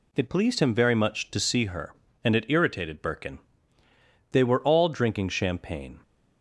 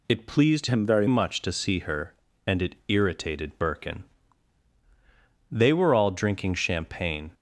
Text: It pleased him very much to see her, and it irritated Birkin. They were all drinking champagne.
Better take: first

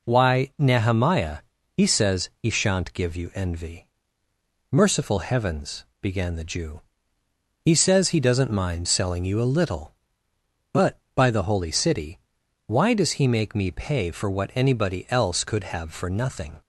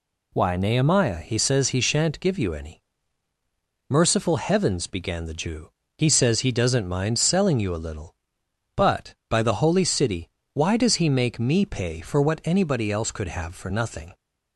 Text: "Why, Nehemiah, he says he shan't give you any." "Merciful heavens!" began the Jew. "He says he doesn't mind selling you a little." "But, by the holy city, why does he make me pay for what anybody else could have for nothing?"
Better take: second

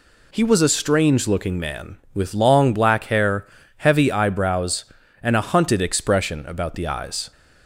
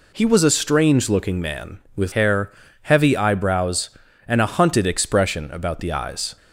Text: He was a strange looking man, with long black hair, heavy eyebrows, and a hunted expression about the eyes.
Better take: first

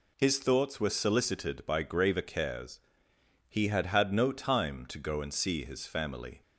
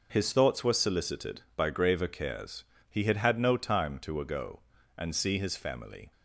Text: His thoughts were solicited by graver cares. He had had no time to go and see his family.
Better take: first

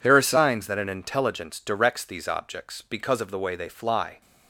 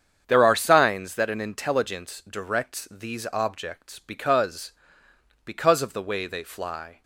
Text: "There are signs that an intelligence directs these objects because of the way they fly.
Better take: first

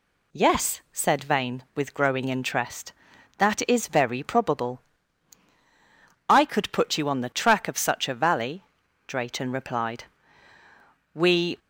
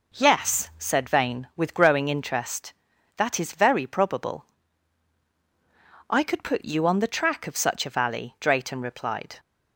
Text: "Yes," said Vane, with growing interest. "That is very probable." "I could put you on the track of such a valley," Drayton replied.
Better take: second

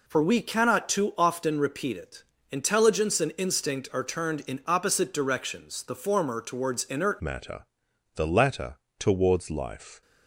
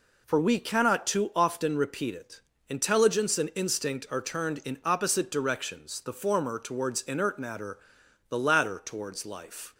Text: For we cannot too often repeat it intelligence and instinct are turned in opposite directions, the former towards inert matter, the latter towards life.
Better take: second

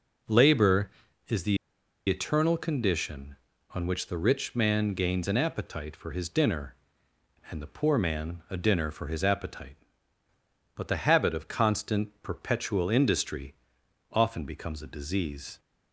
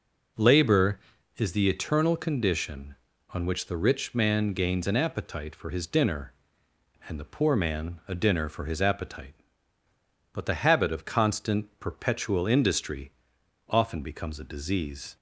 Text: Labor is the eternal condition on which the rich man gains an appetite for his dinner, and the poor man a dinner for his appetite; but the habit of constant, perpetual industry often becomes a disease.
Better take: second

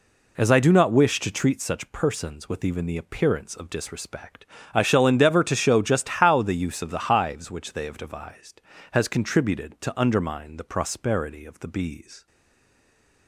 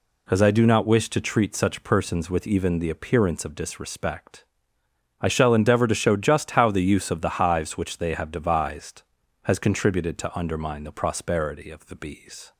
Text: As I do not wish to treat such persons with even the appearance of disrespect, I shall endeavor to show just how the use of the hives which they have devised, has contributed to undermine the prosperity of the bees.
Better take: second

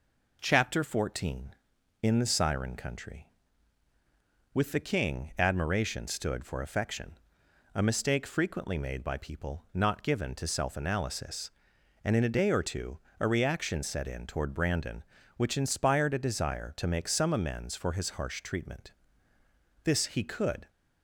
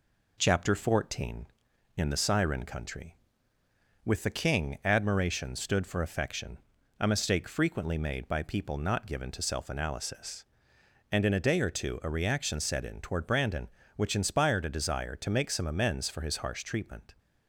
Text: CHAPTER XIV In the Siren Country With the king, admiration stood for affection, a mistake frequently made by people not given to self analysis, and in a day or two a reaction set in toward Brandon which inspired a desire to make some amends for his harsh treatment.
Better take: second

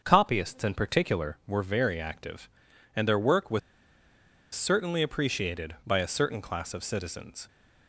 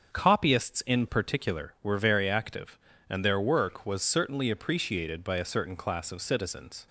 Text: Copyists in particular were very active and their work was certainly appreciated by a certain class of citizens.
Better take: second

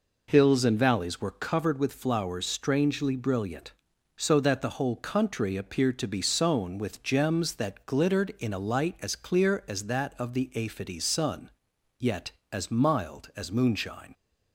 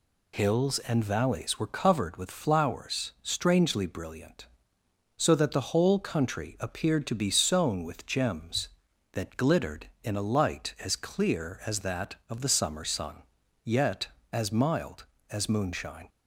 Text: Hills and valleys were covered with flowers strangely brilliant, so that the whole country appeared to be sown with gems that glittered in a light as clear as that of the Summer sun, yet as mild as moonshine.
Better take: second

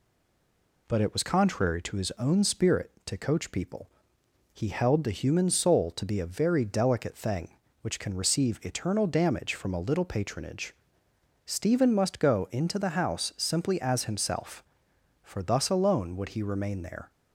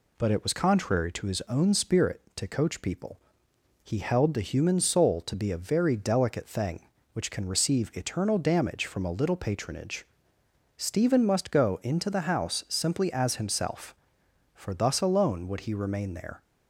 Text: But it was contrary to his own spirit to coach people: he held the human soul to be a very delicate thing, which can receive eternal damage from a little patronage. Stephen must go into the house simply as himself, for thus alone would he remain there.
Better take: second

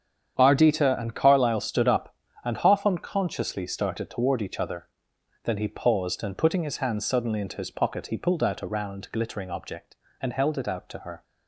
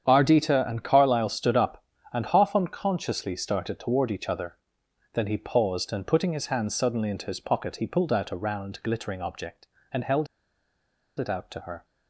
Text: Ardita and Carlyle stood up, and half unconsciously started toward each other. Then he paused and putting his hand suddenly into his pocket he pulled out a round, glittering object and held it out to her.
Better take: first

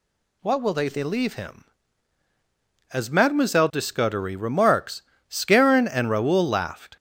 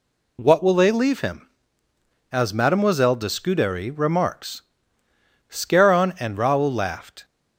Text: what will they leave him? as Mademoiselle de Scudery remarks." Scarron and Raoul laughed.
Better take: second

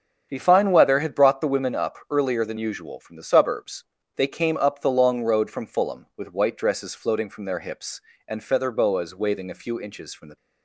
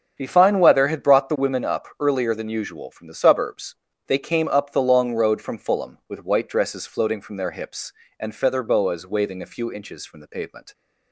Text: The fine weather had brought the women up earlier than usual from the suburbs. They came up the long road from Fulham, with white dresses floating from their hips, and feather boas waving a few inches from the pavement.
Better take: second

